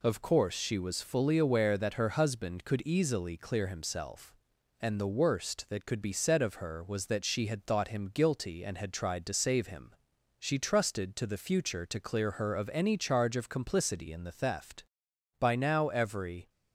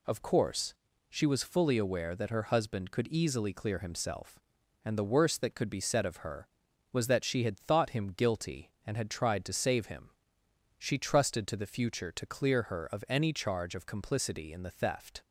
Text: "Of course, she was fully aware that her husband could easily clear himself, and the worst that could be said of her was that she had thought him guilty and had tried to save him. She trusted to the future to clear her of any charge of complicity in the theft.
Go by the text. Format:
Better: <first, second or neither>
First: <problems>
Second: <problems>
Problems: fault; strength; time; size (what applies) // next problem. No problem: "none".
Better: second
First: goes on to say "By now every"; noticeable; from 15.3 s on; 1.1 s long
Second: none